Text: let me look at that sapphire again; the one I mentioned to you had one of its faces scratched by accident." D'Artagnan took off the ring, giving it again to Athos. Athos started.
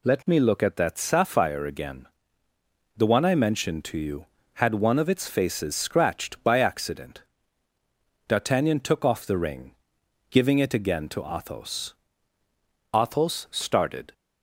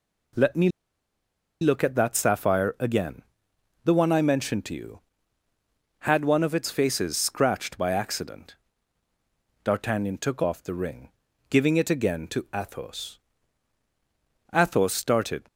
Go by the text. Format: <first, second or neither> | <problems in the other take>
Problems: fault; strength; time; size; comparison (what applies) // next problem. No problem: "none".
first | pauses between "me" and "look"; noticeable; at 0.6 s; 0.93 s long